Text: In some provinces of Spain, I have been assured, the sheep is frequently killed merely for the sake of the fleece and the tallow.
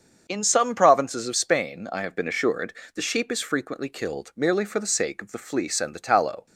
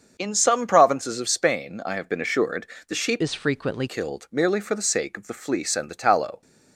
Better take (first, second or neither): first